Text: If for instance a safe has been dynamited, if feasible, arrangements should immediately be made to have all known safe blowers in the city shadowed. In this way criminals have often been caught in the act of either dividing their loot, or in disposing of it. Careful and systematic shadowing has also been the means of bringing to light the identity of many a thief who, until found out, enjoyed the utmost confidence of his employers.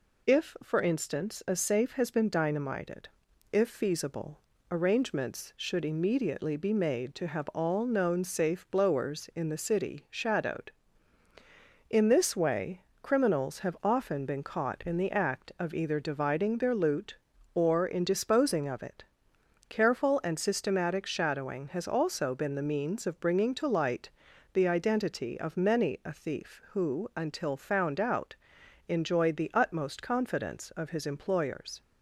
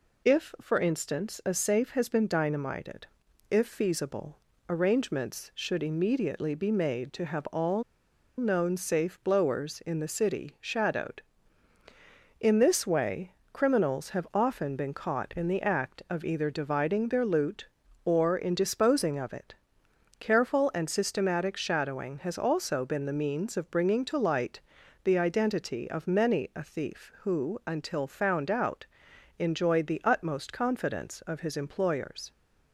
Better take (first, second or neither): first